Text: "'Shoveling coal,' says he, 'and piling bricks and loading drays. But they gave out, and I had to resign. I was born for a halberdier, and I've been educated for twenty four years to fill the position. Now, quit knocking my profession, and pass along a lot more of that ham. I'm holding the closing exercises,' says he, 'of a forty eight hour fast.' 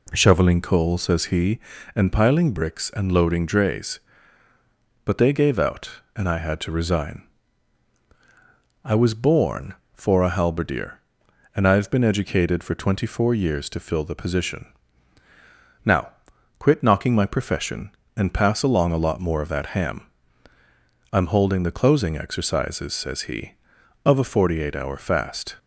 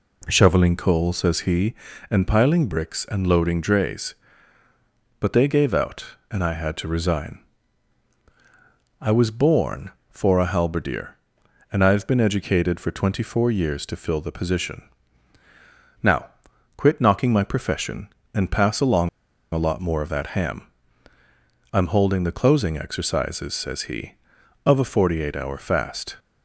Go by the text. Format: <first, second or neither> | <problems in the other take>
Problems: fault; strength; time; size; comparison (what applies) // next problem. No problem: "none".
first | pauses between "along" and "a"; at 19.0 s; 0.44 s long